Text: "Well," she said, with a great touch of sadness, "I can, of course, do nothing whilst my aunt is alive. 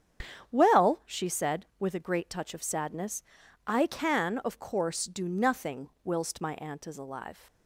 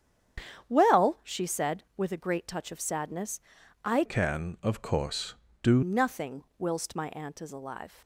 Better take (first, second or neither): first